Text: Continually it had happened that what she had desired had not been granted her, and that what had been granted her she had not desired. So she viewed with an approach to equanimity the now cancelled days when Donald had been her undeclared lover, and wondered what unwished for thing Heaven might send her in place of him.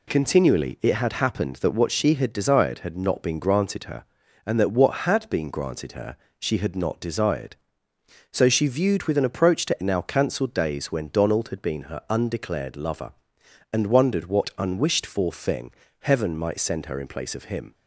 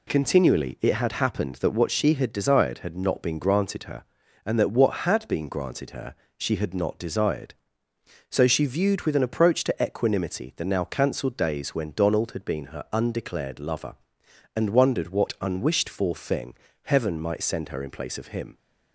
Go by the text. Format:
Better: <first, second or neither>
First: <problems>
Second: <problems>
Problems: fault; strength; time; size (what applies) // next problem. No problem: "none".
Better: second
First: pauses between "her" and "she"; slight; at 6.1 s; 0.22 s long // skips "equanimity the"; at 9.8 s // pauses between "thing" and "Heaven"; slight; at 15.6 s; 0.30 s long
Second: pauses between "her" and "she"; slight; at 6.1 s; 0.22 s long // pauses between "thing" and "Heaven"; slight; at 16.5 s; 0.30 s long